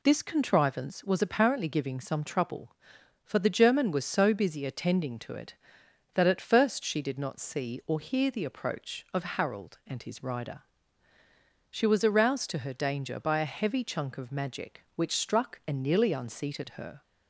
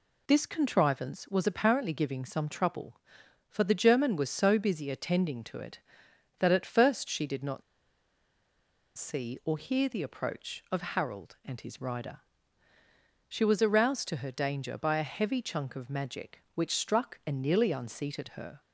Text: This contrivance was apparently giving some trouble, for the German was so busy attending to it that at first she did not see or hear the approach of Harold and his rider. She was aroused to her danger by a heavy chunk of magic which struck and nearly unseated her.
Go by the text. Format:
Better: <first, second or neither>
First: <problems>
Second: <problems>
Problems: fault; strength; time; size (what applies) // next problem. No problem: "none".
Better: first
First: none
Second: pauses between "not" and "see"; strong; at 7.6 s; 1.3 s long